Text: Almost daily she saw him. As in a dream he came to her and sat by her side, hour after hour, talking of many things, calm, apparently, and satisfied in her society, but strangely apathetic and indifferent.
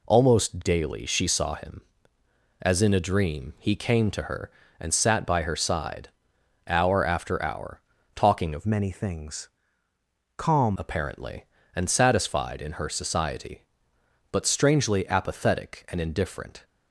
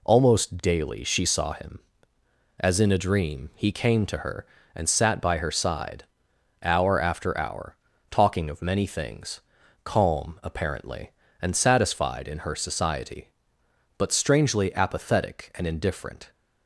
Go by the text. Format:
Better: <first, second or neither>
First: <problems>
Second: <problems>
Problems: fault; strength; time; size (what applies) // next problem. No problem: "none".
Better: second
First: changes voice from "many" to "calm"; from 8.6 to 10.7 s; 2.1 s long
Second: none